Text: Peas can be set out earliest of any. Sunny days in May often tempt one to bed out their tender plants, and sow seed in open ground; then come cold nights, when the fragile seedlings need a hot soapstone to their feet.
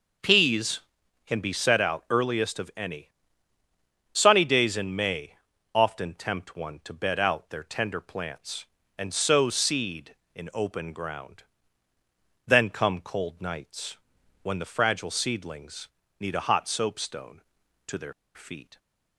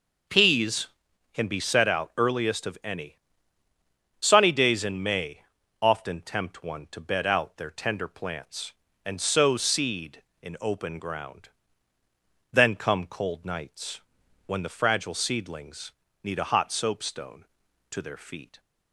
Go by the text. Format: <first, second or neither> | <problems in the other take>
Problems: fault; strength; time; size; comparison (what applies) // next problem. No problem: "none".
second | pauses between "May" and "often"; at 5.3 s; 0.40 s long; also in the second // pauses between "seedlings" and "need"; slight; at 15.8 s; 0.30 s long; slight in the second // pauses between "their" and "feet"; slight; at 18.1 s; 0.22 s long